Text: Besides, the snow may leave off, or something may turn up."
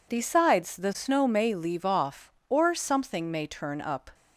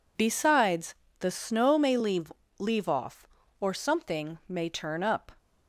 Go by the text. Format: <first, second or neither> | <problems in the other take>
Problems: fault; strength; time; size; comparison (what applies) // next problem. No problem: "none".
first | says "leave" twice; at 2.5 s